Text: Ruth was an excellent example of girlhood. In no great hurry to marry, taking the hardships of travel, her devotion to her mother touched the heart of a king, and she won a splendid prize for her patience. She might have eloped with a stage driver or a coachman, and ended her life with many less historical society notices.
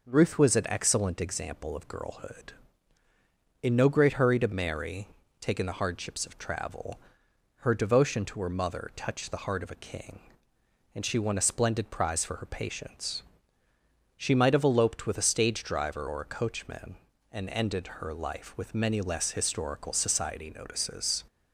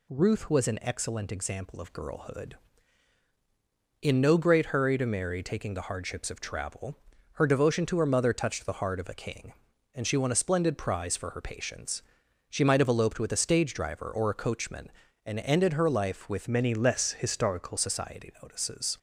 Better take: first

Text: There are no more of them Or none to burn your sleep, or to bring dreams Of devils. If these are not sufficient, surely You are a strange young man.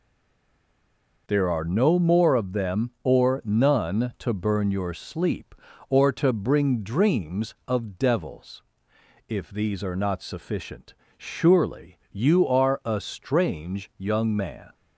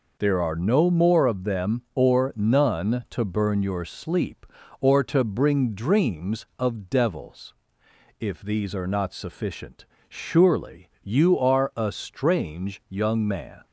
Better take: second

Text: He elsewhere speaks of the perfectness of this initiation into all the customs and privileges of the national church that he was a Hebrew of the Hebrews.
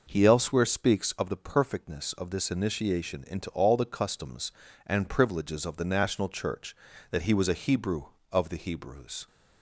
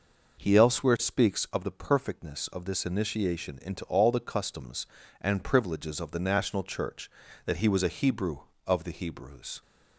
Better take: neither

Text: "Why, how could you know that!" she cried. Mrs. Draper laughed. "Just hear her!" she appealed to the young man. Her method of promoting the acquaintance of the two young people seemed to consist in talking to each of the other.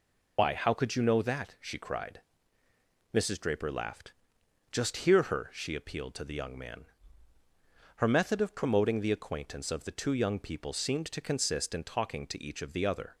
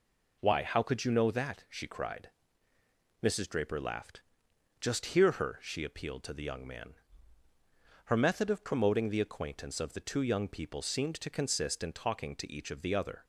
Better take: second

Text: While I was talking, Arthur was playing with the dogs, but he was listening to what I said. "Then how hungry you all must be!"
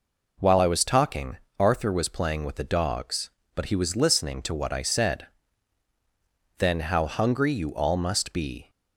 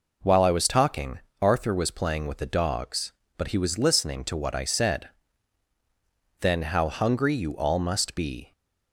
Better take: neither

